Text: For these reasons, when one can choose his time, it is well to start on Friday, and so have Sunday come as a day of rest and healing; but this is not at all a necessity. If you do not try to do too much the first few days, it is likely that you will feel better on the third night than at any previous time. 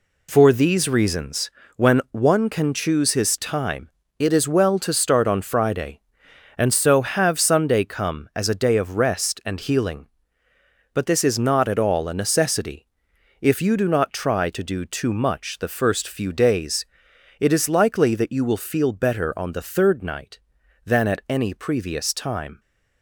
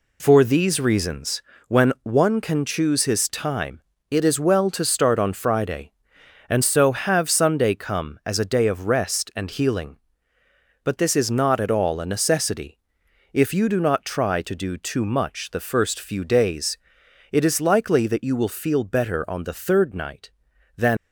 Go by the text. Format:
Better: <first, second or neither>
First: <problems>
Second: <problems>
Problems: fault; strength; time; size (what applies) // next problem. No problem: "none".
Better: first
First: none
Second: stops before "at any previous time"; at 20.9 s